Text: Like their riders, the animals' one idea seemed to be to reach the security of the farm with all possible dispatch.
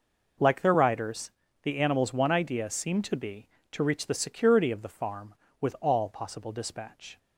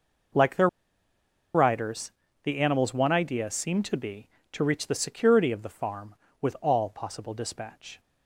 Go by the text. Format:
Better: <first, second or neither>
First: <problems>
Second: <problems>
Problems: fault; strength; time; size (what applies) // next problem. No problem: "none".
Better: first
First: none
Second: pauses between "their" and "riders"; noticeable; at 0.6 s; 0.86 s long